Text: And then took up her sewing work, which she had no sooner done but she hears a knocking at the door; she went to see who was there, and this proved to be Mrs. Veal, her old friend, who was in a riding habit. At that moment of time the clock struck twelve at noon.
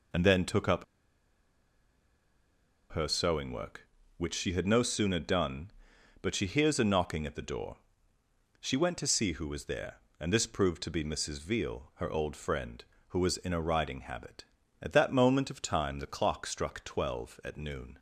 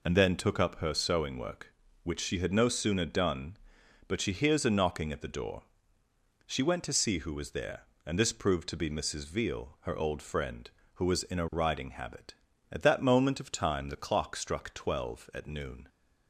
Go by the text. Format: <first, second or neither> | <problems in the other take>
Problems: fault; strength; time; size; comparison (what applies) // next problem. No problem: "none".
second | pauses between "up" and "her"; strong; at 0.8 s; 2.0 s long